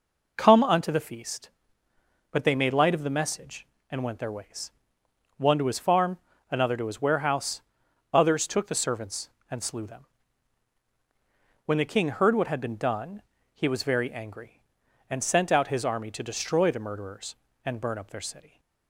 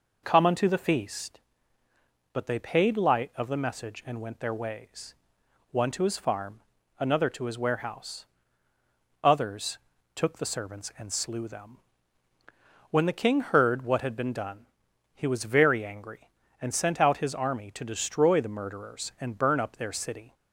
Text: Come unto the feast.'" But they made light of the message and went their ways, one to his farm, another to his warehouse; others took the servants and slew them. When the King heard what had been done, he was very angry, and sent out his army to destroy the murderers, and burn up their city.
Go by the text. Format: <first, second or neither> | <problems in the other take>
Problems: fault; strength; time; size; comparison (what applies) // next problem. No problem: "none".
first | says "paid" for "made"; at 2.6 s // pauses between "others" and "took"; at 9.7 s; 0.38 s long